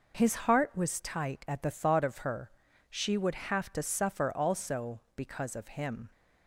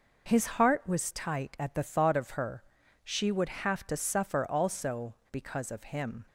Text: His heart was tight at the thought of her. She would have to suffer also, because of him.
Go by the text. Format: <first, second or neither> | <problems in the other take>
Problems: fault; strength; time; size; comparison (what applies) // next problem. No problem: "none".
neither | none